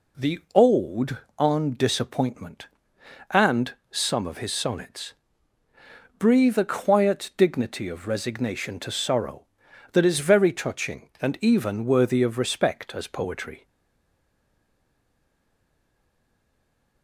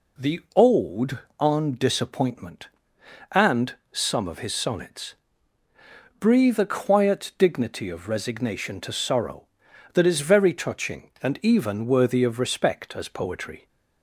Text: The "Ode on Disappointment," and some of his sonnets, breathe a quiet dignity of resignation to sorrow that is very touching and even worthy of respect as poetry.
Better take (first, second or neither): second